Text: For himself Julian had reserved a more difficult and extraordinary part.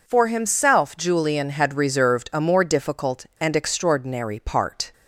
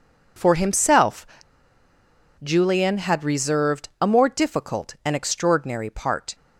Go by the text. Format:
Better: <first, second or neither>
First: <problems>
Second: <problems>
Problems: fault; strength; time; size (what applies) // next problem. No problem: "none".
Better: first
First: none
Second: pauses between "himself" and "Julian"; at 1.2 s; 1.1 s long